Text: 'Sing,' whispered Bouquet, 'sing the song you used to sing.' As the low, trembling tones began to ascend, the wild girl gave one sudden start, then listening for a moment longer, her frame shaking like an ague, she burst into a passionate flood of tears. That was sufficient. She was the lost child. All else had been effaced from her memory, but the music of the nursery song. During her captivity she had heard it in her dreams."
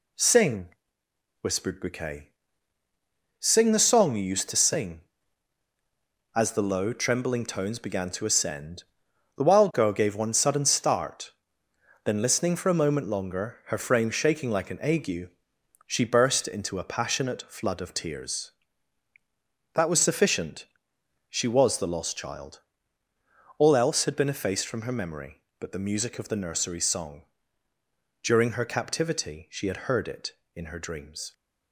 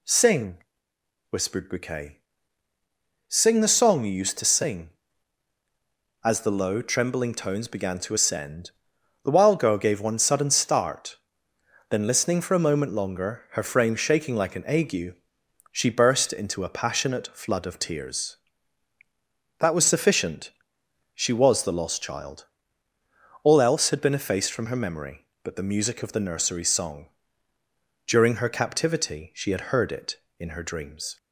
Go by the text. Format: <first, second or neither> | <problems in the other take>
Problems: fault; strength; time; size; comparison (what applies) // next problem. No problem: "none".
second | gets quieter; noticeable; throughout; 5 dB